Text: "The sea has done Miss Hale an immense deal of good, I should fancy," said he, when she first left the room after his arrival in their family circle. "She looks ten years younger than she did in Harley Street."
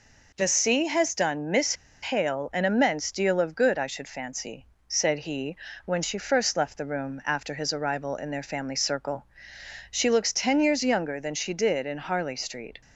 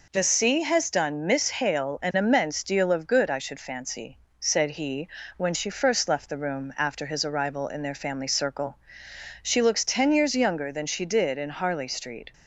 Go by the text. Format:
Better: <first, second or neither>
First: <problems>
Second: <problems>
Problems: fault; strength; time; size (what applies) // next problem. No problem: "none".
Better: second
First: pauses between "Miss" and "Hale"; slight; at 1.7 s; 0.28 s long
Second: none